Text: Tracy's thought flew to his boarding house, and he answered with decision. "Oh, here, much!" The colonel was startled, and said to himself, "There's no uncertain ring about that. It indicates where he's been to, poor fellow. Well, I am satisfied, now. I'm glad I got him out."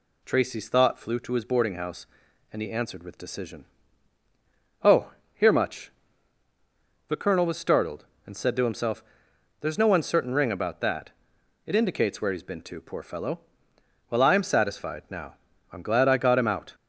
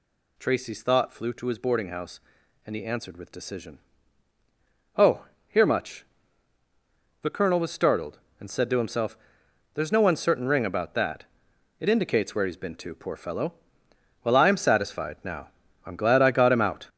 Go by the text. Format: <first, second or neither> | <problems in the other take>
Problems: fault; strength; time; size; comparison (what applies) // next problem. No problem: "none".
first | gets louder; strong; throughout; 7 dB